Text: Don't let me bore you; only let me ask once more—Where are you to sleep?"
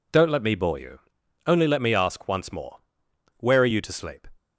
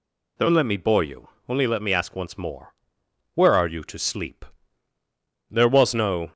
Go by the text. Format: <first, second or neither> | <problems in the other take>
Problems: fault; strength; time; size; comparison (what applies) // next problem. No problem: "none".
first | goes on to say "There was no"; noticeable; from 5.5 s on; 0.82 s long